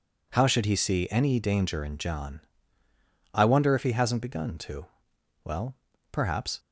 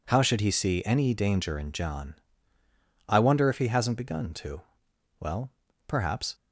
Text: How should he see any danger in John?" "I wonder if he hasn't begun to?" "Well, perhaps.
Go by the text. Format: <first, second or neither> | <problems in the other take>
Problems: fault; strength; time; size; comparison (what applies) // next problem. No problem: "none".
neither | none